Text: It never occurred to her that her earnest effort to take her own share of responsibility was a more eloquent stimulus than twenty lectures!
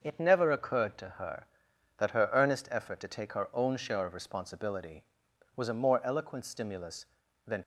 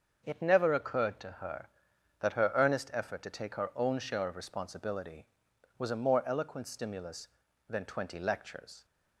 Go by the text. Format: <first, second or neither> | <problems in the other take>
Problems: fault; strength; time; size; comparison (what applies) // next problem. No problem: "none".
second | starts louder than the rest; until 1.0 s; 6.5 dB; also in the second // stops before "twenty lectures"; at 7.6 s